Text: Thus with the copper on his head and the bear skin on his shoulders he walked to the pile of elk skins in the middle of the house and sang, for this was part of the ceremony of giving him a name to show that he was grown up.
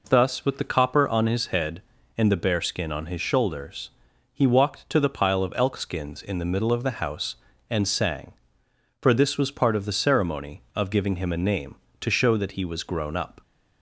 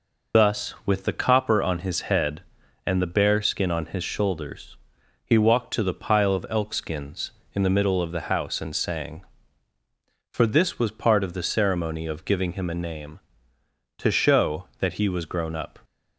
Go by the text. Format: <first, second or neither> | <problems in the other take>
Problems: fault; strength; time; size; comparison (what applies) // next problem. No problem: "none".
first | loses the start of "Thus"; at 0.3 s; 60 ms // pauses between "shoulders" and "he"; noticeable; at 4.7 s; 0.48 s long; also in the first